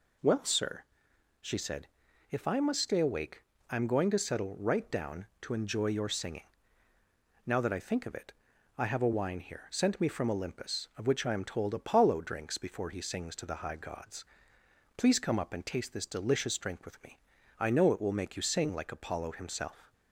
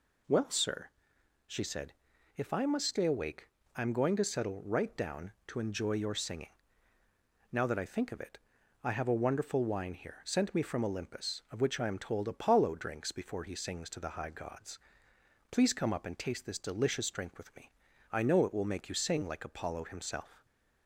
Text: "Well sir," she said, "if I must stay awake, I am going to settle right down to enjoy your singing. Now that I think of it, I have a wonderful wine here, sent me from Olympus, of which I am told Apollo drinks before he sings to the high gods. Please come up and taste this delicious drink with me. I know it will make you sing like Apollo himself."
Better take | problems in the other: second | skips "wonderful"; at 9.1 s

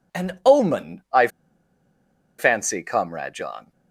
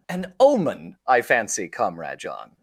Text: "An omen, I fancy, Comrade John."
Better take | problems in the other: second | pauses between "I" and "fancy"; at 1.2 s; 1.1 s long

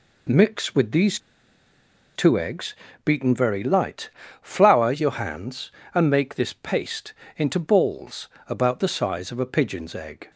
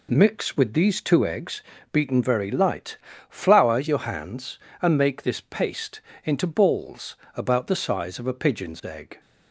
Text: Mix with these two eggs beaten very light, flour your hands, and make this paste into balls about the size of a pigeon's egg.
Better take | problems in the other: second | pauses between "these" and "two"; noticeable; at 1.1 s; 0.97 s long // pauses between "eggs" and "beaten"; slight; at 2.7 s; 0.30 s long; slight in the second // pauses between "paste" and "into"; slight; at 7.1 s; 0.24 s long; slight in the second // pauses between "balls" and "about"; slight; at 8.2 s; 0.20 s long; slight in the second

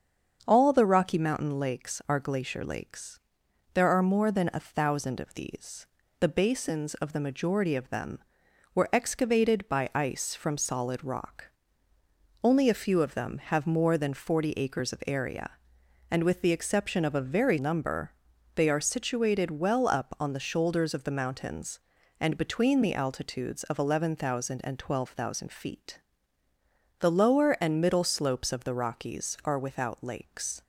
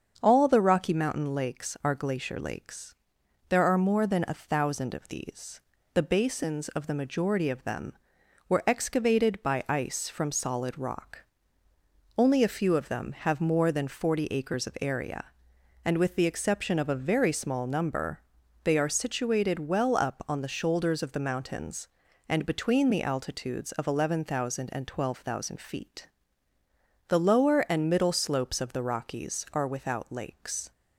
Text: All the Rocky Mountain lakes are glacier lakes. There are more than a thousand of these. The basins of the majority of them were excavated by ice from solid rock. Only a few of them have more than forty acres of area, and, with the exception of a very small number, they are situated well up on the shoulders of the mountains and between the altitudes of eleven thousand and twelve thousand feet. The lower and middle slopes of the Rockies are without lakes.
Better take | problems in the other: second | starts louder than the rest; until 1.4 s; 7 dB; also in the second // skips "small"; at 17.5 s

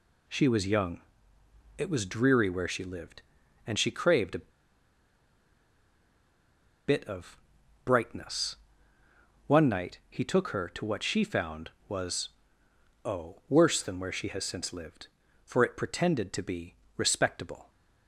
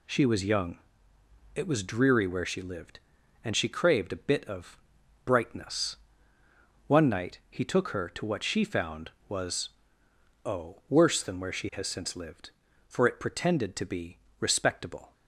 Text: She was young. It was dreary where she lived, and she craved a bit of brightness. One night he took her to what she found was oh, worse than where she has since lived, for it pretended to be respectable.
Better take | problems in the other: second | pauses between "a" and "bit"; strong; at 4.5 s; 2.3 s long // pauses between "of" and "brightness"; noticeable; at 7.3 s; 0.46 s long; noticeable in the second // pauses between "was" and "oh"; noticeable; at 12.2 s; 0.76 s long; noticeable in the second // pauses between "be" and "respectable"; slight; at 16.7 s; 0.20 s long; slight in the second

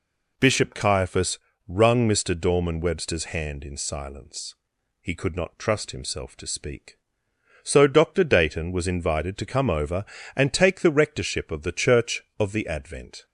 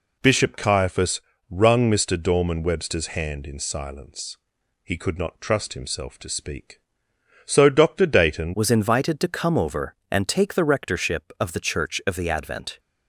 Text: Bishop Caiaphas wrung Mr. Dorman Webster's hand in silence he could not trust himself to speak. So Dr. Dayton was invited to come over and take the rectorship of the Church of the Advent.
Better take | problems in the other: first | pauses between "Caiaphas" and "wrung"; slight; at 1.2 s; 0.28 s long; slight in the first // pauses between "silence" and "he"; noticeable; at 4.3 s; 0.46 s long; noticeable in the first // changes voice at "was"; from 8.5 s on; 4.2 s long

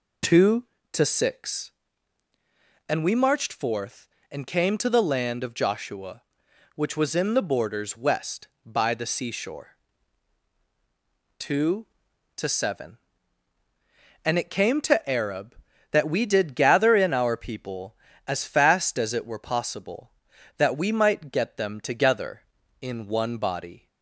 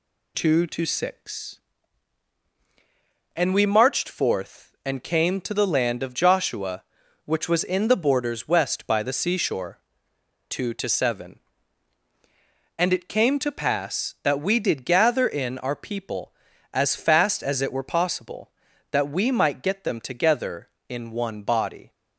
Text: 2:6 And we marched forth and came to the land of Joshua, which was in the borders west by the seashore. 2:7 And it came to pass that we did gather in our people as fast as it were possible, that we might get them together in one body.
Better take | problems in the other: second | says "arab" for "pass"; at 15.0 s

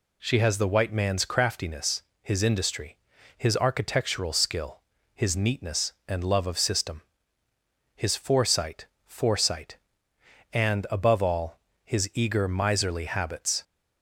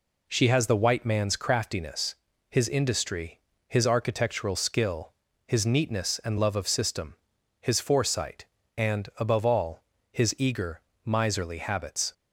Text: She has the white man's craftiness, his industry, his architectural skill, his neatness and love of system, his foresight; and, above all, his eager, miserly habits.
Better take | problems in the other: second | says "foresight" twice; at 9.0 s

